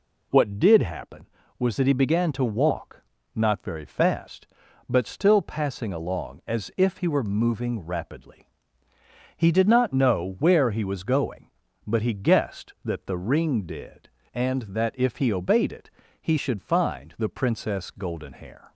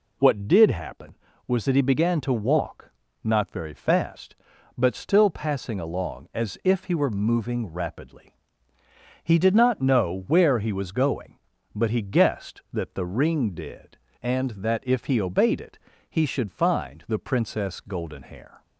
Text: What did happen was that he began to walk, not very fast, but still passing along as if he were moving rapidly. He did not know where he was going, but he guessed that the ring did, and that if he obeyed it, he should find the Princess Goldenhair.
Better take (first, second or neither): neither